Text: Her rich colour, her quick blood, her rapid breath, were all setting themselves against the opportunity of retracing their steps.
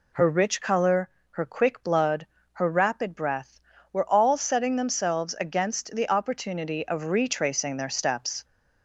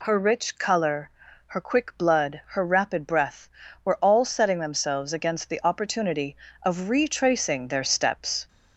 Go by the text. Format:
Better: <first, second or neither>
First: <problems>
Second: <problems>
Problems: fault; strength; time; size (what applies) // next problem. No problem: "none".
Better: neither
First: none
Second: none